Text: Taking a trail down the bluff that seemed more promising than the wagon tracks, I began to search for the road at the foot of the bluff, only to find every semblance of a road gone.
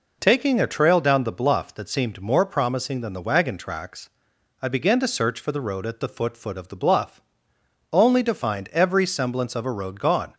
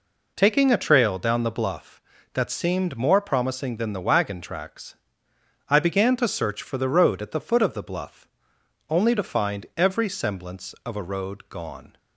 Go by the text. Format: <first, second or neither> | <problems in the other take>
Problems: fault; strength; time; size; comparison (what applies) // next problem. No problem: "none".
second | says "foot" twice; at 6.3 s